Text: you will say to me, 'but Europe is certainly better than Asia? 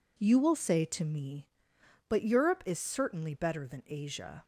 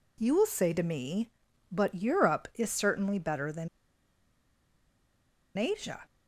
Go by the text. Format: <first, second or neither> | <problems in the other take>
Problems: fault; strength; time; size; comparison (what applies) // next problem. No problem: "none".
first | pauses between "than" and "Asia"; strong; at 3.6 s; 1.8 s long